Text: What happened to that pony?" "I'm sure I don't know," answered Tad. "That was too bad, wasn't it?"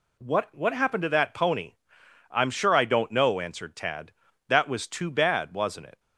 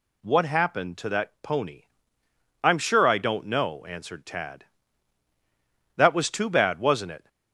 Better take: second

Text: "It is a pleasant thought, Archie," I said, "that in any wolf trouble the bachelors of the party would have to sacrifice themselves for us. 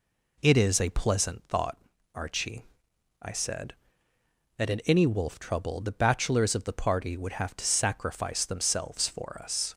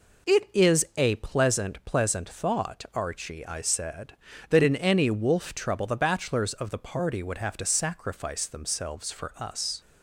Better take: first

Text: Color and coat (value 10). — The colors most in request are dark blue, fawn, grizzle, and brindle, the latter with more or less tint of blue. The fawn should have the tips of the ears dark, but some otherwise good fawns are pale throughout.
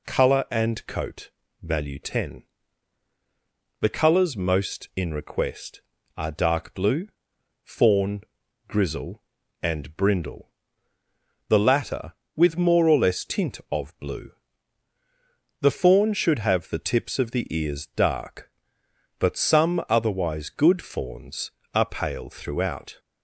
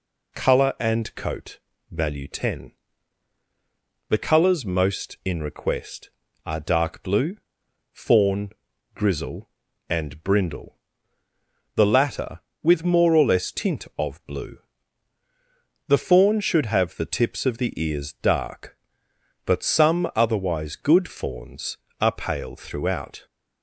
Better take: neither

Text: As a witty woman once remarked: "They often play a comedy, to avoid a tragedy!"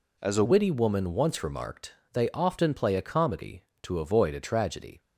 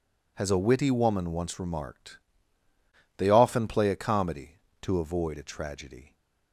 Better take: second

